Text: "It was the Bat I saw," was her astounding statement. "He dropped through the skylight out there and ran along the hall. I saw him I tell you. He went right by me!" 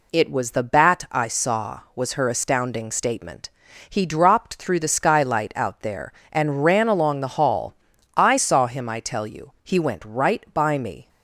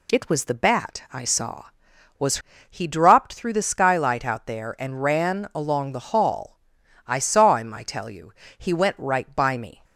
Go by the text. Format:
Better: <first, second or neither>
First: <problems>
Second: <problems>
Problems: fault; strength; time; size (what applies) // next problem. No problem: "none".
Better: first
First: none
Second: skips "her astounding statement"; at 2.5 s